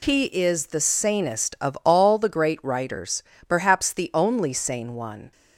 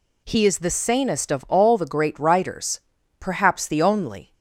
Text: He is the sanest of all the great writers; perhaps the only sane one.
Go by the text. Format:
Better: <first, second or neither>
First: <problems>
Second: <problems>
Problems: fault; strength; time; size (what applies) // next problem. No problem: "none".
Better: first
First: none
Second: stops before "sane one"; at 4.3 s